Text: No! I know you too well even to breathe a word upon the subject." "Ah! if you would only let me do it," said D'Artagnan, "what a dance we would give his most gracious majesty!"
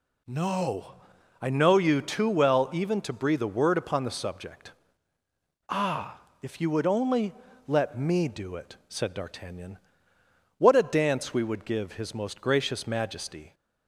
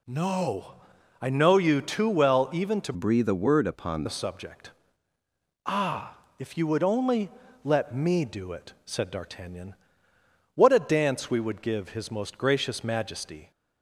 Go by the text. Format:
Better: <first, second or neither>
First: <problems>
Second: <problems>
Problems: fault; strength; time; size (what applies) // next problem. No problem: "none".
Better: first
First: pauses between "only" and "let"; slight; at 7.3 s; 0.36 s long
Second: changes voice from "breathe" to "upon"; from 2.9 to 4.0 s; 1.1 s long // pauses between "only" and "let"; slight; at 7.2 s; 0.36 s long